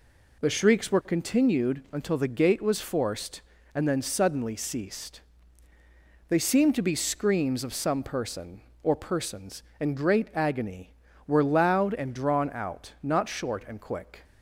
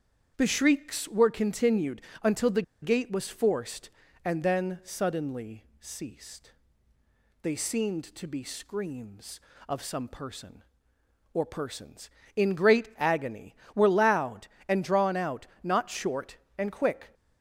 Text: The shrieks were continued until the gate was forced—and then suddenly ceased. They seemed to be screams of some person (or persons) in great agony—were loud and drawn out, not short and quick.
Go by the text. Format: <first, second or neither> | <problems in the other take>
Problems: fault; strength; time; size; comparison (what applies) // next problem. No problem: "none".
first | starts louder than the rest; strong; until 1.3 s; 8 dB // pauses between "continued" and "until"; slight; at 2.0 s; 0.22 s long // pauses between "the" and "gate"; slight; at 2.6 s; 0.19 s long // pauses between "suddenly" and "ceased"; slight; at 5.6 s; 0.16 s long